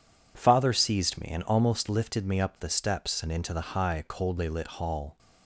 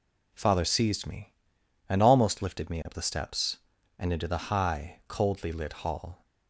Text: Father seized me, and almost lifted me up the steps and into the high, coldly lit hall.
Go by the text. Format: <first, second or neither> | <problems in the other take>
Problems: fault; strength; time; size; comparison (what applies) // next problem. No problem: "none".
neither | none